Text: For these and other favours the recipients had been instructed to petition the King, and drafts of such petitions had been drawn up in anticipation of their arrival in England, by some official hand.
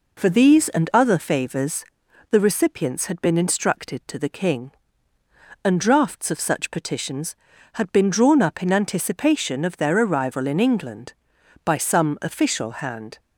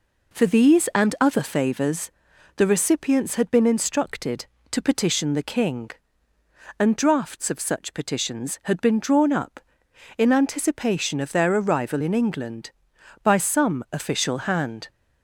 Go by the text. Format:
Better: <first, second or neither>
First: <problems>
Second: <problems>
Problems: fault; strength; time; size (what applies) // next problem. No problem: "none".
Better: second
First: pauses between "favours" and "the"; noticeable; at 1.8 s; 0.46 s long // skips "petition"; at 4.1 s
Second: pauses between "favours" and "the"; noticeable; at 2.0 s; 0.46 s long